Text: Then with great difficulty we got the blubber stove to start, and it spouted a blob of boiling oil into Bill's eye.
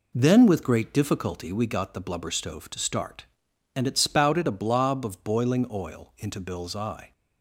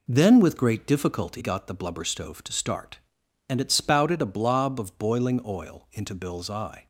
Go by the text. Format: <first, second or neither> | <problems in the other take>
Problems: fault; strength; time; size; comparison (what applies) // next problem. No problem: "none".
first | skips "we"; at 1.4 s